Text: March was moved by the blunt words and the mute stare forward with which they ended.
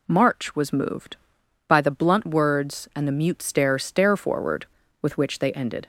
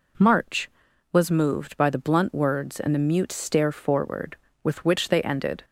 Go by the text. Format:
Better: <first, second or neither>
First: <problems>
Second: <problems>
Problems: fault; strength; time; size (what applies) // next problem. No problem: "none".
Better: second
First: says "stare" twice; at 3.7 s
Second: none